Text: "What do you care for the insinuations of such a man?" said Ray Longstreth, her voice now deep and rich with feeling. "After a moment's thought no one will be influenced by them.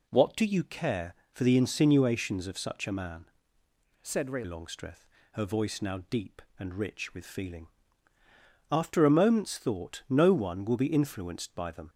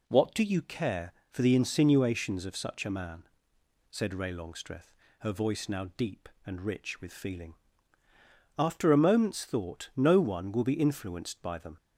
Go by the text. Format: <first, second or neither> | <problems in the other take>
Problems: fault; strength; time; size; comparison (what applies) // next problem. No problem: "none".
second | changes voice from "said" to "Ray"; from 4.0 to 4.4 s; 0.4 s long